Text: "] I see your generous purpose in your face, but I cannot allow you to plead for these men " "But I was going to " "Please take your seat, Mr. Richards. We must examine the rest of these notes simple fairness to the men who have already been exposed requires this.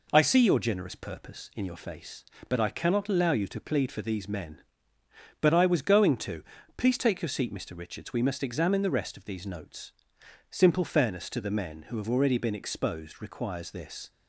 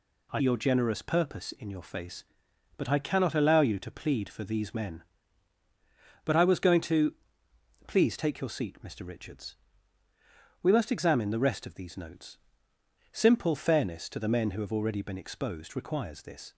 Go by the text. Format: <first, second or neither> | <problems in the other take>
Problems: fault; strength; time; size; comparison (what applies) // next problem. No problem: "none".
first | skips "see"; at 0.4 s // pauses between "notes" and "simple"; noticeable; at 12.3 s; 0.74 s long; noticeable in the first